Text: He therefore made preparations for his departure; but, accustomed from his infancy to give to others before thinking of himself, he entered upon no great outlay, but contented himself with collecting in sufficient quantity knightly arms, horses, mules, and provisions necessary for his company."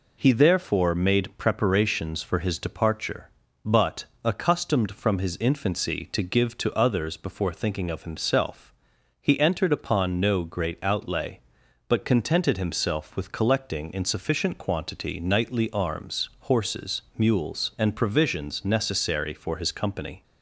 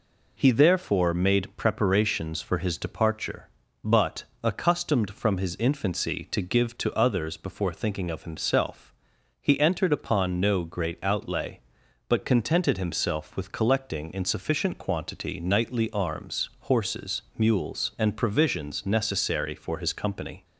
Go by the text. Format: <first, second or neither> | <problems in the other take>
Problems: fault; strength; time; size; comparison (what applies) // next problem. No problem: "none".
neither | none